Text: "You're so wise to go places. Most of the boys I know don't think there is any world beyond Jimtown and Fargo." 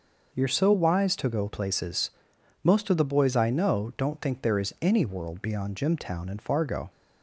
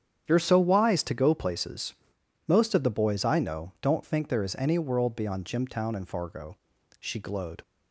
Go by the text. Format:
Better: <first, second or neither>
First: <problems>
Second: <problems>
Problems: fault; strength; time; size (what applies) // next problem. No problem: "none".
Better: first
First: none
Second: starts louder than the rest; strong; until 1.2 s; 9 dB // goes on to say "She glowed"; noticeable; from 6.9 s on; 0.62 s long